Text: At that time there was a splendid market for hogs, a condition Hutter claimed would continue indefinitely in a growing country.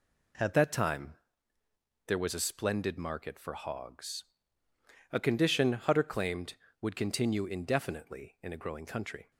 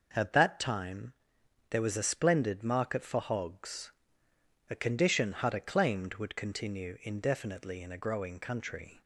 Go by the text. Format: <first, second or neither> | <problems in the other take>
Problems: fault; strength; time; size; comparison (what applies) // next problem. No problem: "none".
second | changes voice at "that"; from 0.5 s on; 8.8 s long // pauses between "time" and "there"; noticeable; at 1.1 s; 0.92 s long; noticeable in the second